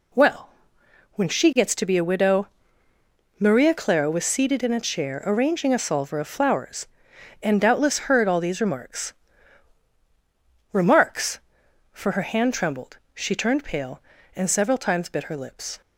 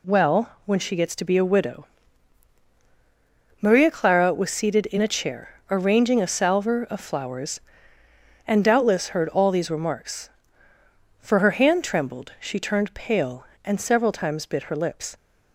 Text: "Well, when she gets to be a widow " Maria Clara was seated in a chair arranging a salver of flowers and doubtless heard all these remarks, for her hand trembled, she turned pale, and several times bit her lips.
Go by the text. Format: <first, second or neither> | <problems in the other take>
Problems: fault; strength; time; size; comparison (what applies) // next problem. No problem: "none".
second | says "remarks" twice; at 10.7 s